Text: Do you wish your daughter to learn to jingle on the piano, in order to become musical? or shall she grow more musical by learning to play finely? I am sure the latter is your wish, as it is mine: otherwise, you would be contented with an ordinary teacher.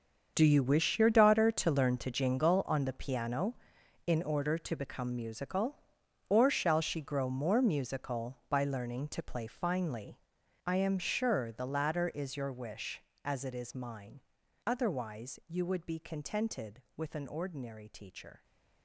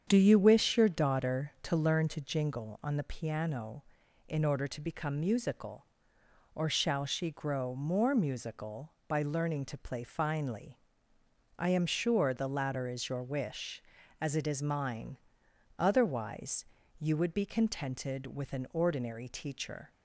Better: second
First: gets quieter; strong; throughout; 14 dB // starts louder than the rest; until 1.3 s; 7 dB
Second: starts louder than the rest; strong; until 1.0 s; 8 dB

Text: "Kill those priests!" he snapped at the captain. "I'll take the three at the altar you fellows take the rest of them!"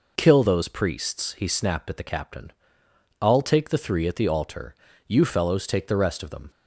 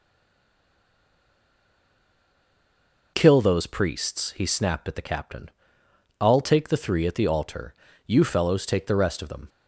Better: first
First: pauses between "altar" and "you"; slight; at 4.7 s; 0.32 s long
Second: stays silent before the first word; strong; until 3.1 s; 3.1 s long // pauses between "altar" and "you"; slight; at 7.7 s; 0.32 s long

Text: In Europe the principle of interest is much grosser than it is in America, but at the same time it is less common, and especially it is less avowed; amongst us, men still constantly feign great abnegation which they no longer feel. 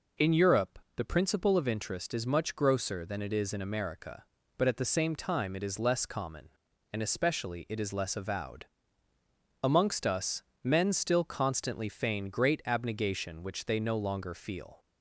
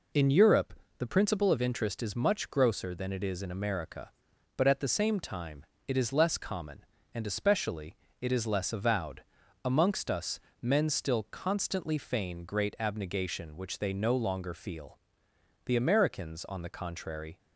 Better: first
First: pauses between "Europe" and "the"; slight; at 0.8 s; 0.16 s long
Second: pauses between "Europe" and "the"; slight; at 0.7 s; 0.24 s long // pauses between "time" and "it"; slight; at 5.6 s; 0.24 s long // pauses between "especially" and "it"; slight; at 7.9 s; 0.24 s long // goes on to say "The Americans on the contrary"; strong; from 15.6 s on; 1.7 s long

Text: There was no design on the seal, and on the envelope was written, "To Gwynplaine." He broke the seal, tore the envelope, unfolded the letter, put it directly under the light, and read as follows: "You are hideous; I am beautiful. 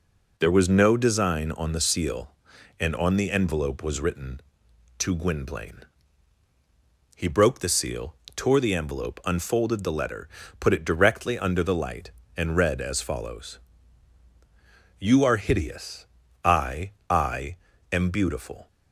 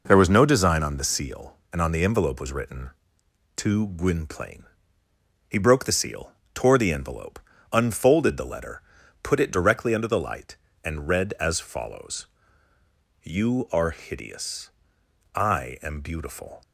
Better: second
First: says "I" twice; at 17.0 s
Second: none

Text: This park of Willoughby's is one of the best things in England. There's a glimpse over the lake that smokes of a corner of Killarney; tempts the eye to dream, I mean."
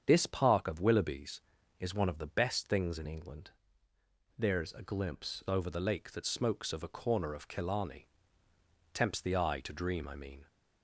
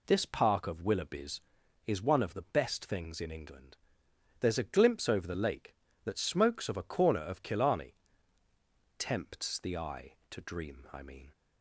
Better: second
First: starts louder than the rest; strong; until 1.0 s; 7.5 dB // changes voice from "England" to "glimpse"; from 3.0 to 5.4 s; 2.4 s long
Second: none

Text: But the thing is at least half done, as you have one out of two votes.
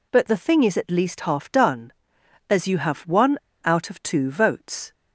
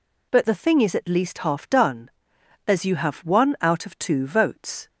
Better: second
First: pauses between "one" and "out"; slight; at 3.3 s; 0.27 s long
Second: none

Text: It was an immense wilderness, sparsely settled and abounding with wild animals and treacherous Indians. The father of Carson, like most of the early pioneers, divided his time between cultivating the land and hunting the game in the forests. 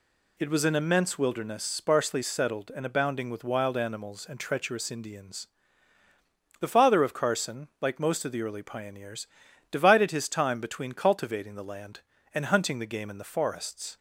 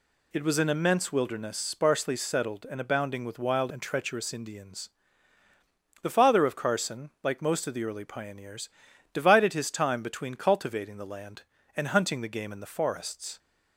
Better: first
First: none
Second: skips "animals"; at 3.7 s

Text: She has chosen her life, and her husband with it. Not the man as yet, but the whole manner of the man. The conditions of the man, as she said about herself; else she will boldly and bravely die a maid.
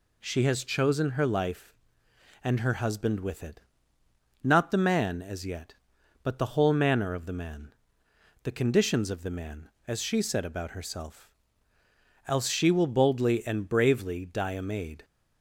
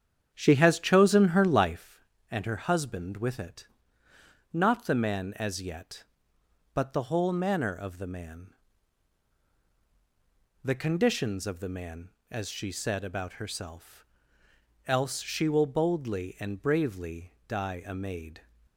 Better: first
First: none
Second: starts louder than the rest; strong; until 1.8 s; 8.5 dB

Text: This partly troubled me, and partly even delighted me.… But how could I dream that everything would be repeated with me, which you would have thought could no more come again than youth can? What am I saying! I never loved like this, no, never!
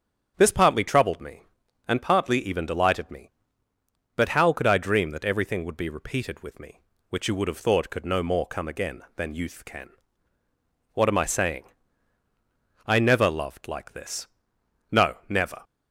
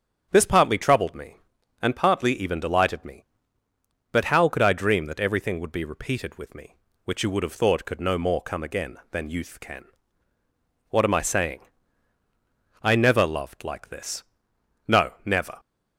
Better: neither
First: starts louder than the rest; strong; until 1.3 s; 7.5 dB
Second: starts louder than the rest; strong; until 1.3 s; 7.5 dB

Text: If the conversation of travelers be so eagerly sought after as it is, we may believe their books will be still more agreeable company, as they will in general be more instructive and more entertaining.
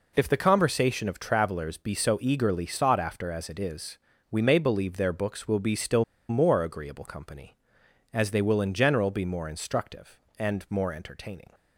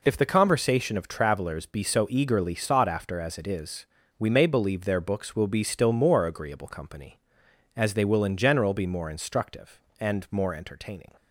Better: second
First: pauses between "still" and "more"; slight; at 6.0 s; 0.25 s long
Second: none

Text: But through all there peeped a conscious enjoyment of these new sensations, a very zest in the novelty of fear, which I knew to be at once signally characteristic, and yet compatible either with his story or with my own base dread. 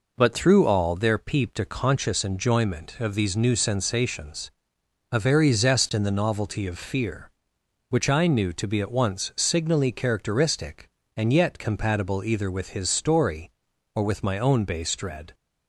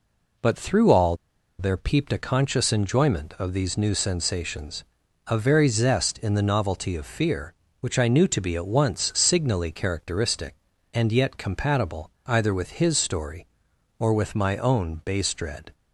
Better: first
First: none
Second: pauses between "all" and "there"; at 1.1 s; 0.43 s long // pauses between "compatible" and "either"; slight; at 12.0 s; 0.16 s long

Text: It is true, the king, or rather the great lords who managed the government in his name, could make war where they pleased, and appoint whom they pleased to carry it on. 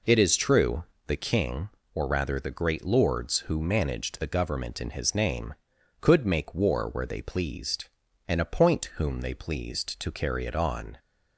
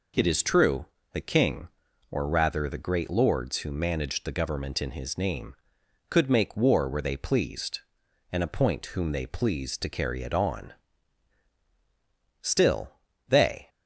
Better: first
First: none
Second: goes on to say "Still they"; noticeable; from 12.4 s on; 1.2 s long

